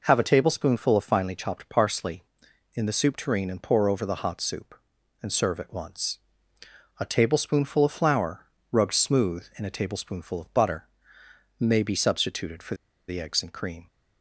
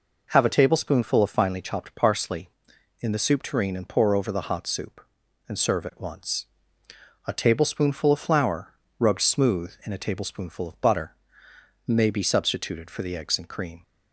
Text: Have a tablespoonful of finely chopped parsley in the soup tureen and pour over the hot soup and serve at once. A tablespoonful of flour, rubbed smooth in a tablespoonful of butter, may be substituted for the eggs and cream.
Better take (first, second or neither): second